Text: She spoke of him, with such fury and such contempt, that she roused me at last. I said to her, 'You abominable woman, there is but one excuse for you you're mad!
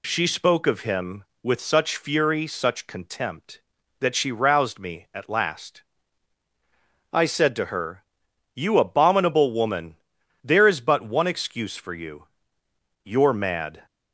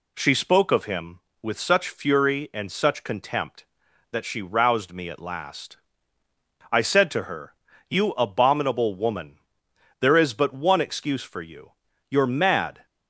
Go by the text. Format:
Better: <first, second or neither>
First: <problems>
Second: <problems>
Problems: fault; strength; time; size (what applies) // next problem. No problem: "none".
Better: second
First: skips "and"; at 2.4 s // pauses between "you" and "you're"; noticeable; at 12.2 s; 0.76 s long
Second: pauses between "you" and "you're"; slight; at 11.7 s; 0.36 s long